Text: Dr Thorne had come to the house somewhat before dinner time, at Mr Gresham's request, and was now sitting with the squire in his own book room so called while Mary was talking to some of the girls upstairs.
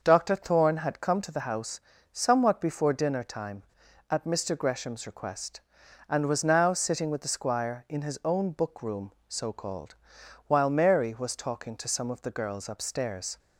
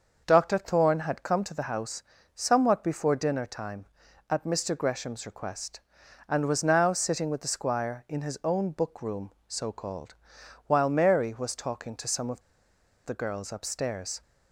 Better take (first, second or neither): first